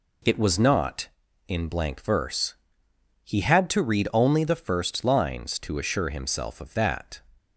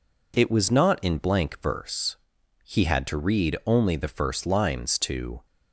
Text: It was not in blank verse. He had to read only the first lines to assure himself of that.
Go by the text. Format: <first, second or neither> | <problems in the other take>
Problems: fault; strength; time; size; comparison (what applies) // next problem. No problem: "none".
first | stops before "assure himself of that"; at 5.4 s